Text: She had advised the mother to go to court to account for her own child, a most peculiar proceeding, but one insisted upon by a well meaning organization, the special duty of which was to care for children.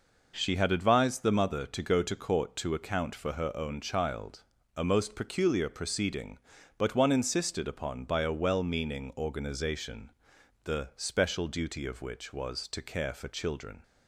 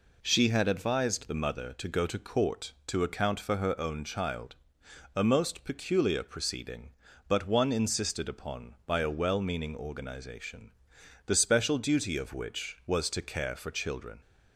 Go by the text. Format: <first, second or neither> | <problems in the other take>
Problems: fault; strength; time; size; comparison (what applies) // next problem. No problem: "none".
neither | none